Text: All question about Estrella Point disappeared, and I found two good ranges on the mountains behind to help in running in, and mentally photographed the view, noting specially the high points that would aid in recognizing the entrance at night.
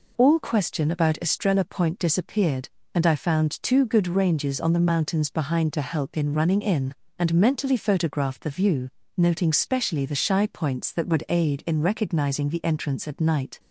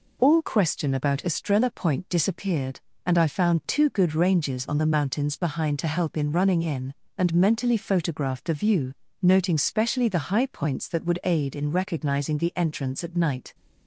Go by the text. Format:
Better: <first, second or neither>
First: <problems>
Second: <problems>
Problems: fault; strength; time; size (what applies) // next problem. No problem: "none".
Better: second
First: says "shy" for "high"; at 10.1 s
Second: none